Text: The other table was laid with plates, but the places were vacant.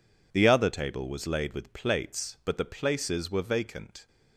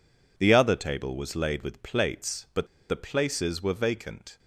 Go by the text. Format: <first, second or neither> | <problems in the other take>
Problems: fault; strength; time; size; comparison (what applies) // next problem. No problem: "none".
first | pauses between "but" and "the"; slight; at 2.6 s; 0.22 s long